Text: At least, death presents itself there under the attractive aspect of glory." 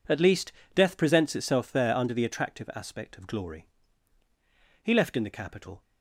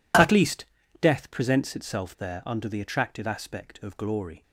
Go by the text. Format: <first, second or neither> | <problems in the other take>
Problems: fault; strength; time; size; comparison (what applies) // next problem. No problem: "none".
second | goes on to say "He left in the capital"; noticeable; from 4.8 s on; 1.0 s long